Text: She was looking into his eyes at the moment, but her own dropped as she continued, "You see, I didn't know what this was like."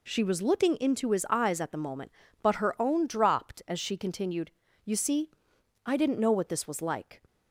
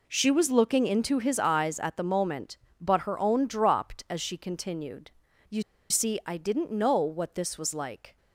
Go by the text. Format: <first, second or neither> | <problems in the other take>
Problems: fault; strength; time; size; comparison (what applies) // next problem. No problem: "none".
first | pauses between "You" and "see"; slight; at 5.6 s; 0.27 s long